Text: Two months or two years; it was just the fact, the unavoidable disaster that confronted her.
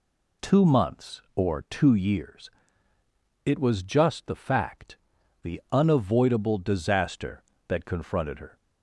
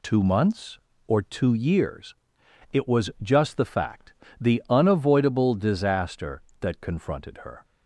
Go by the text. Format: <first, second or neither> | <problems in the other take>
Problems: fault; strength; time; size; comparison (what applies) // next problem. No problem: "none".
neither | none